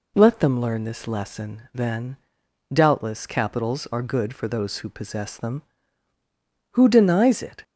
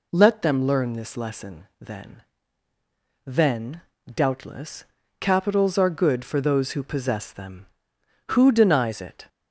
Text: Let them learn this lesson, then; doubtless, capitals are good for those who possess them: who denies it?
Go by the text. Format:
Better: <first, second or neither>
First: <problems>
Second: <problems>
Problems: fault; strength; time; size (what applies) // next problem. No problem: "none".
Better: first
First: none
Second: says "then" twice; at 3.2 s